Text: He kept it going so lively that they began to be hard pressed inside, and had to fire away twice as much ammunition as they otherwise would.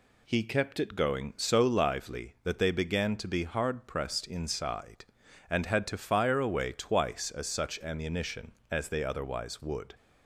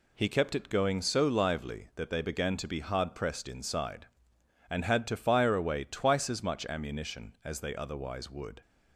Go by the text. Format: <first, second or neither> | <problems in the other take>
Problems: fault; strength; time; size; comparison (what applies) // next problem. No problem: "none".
second | says "such" for "much"; at 7.4 s